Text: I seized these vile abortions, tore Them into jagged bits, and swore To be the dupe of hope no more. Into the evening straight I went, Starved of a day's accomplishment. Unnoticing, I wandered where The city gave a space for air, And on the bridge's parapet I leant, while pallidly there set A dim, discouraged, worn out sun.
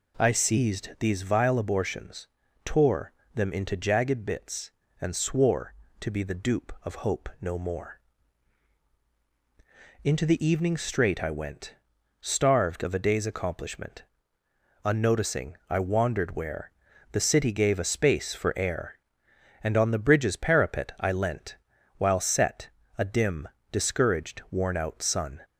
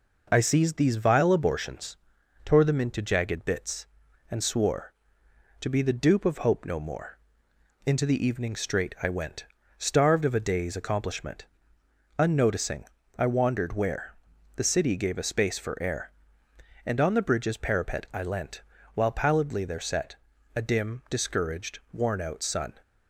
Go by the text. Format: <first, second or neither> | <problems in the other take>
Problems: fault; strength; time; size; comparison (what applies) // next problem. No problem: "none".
second | pauses between "tore" and "Them"; slight; at 3.1 s; 0.22 s long // pauses between "where" and "The"; at 16.7 s; 0.40 s long; also in the second // skips "pallidly there"; at 22.2 s // pauses between "set" and "A"; slight; at 22.6 s; 0.28 s long; also in the second